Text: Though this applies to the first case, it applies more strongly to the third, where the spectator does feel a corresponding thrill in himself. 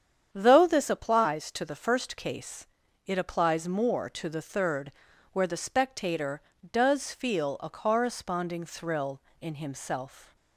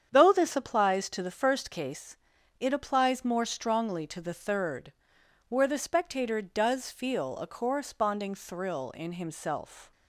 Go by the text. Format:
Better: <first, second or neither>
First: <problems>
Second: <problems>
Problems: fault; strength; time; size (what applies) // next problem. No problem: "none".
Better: second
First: starts louder than the rest; strong; until 1.3 s; 8.5 dB // skips "strongly"; at 4.0 s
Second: starts louder than the rest; strong; until 1.1 s; 8 dB